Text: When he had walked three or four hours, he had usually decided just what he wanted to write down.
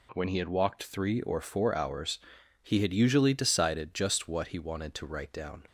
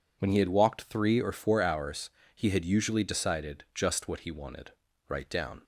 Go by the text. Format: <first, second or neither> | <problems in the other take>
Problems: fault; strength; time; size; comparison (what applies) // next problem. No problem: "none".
first | skips "to"; at 4.9 s